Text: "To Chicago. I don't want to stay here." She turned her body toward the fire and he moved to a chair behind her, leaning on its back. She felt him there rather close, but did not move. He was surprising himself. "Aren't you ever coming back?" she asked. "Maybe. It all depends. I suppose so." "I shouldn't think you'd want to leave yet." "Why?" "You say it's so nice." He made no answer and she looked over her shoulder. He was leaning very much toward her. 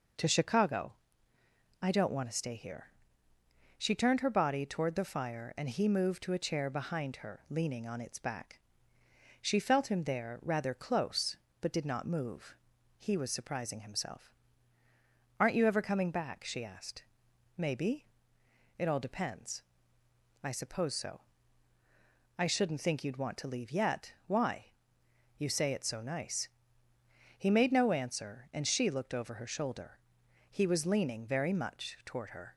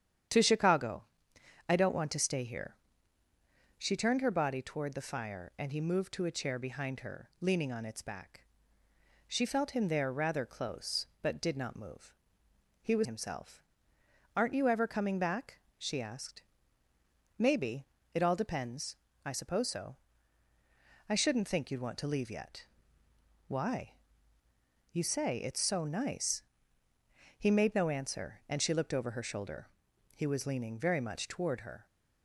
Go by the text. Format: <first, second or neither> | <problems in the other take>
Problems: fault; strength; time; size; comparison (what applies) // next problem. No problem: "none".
first | starts louder than the rest; strong; until 1.9 s; 9 dB // skips "surprising"; at 13.0 s